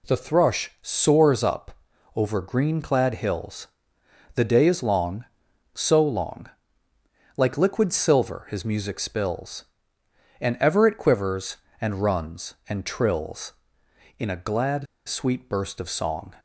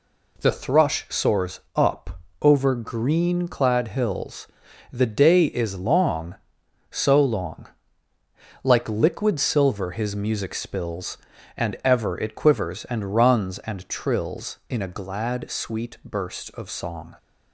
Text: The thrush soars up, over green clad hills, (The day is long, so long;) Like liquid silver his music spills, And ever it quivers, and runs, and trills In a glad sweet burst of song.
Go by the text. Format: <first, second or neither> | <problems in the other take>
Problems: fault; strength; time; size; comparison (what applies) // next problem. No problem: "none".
second | pauses between "glad" and "sweet"; slight; at 14.8 s; 0.21 s long